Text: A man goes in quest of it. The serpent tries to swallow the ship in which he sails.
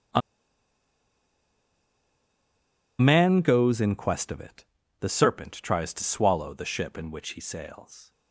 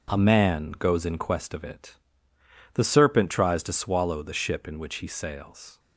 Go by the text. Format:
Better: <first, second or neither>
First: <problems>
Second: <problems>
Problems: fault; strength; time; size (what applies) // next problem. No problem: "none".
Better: second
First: pauses between "A" and "man"; strong; at 0.2 s; 2.7 s long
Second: none